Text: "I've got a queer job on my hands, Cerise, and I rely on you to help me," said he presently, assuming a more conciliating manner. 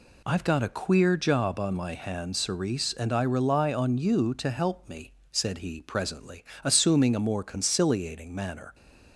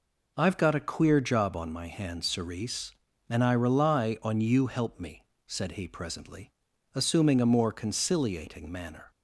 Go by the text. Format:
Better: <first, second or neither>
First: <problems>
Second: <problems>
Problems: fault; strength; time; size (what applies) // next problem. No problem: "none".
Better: first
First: none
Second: skips "to"; at 4.6 s